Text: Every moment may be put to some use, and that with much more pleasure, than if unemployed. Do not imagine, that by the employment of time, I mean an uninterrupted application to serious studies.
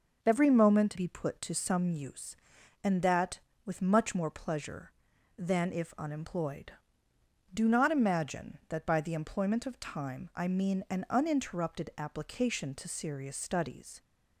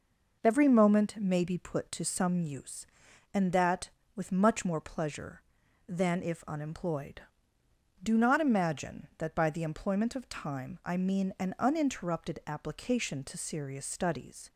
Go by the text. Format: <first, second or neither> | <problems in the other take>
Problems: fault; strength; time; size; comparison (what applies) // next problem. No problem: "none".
second | skips "may"; at 0.9 s